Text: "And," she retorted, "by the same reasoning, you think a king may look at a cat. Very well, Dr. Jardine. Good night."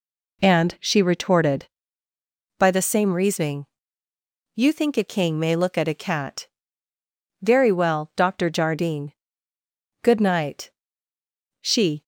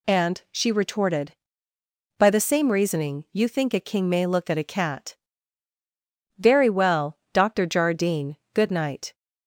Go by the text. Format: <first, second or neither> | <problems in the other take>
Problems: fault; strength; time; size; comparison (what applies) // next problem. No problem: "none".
second | goes on to say "She"; slight; from 11.6 s on; 0.42 s long